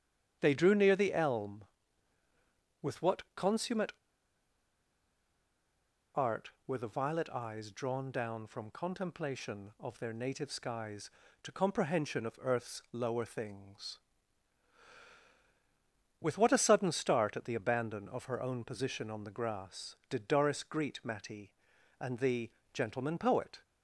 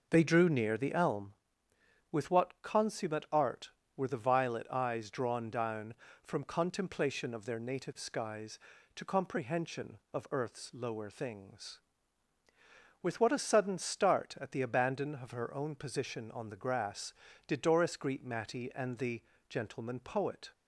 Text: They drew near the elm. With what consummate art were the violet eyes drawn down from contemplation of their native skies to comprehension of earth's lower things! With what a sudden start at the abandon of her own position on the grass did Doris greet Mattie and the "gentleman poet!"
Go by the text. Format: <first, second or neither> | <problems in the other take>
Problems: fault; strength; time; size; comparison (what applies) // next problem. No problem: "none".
second | starts louder than the rest; strong; until 1.4 s; 8.5 dB // pauses between "consummate" and "art"; strong; at 3.9 s; 2.2 s long // pauses between "the" and "gentleman"; slight; at 22.5 s; 0.22 s long; slight in the second